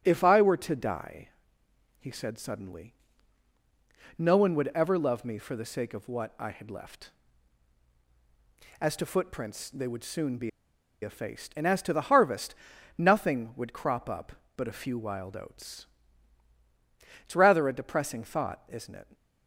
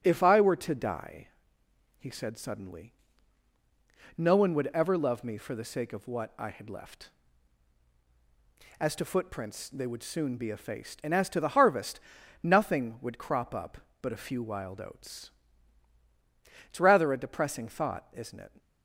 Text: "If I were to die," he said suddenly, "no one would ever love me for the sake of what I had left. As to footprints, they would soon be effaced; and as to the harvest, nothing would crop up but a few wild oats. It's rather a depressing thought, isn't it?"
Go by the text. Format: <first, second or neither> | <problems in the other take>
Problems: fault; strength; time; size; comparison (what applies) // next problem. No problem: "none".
second | starts louder than the rest; until 1.0 s; 6.5 dB; also in the second // pauses between "be" and "effaced"; noticeable; at 10.4 s; 0.53 s long